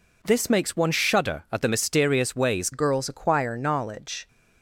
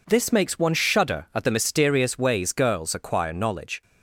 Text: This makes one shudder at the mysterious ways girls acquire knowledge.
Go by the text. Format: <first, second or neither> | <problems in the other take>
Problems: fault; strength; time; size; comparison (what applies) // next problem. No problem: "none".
second | changes voice at "girls"; from 2.7 s on; 1.5 s long